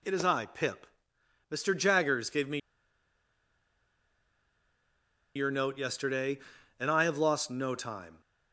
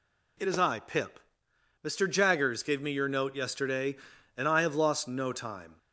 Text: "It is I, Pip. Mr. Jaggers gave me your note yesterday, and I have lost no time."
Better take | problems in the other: second | pauses between "me" and "your"; strong; at 2.5 s; 2.7 s long

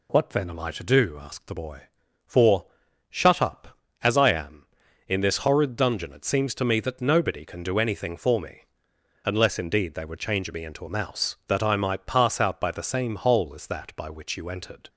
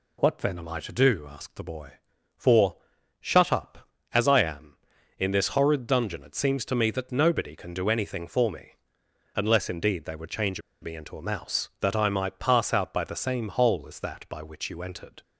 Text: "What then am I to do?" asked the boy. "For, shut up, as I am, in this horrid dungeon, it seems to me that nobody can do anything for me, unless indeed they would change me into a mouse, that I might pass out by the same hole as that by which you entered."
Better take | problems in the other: first | pauses between "change" and "me"; slight; at 10.6 s; 0.20 s long

